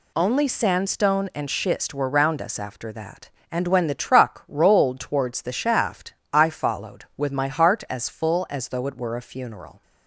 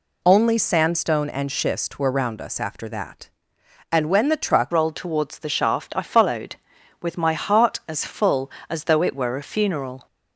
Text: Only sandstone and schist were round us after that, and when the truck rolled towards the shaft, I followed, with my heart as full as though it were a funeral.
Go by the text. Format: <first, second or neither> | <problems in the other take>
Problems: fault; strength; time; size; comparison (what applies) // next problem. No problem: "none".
first | changes voice at "rolled"; from 4.7 s on; 5.3 s long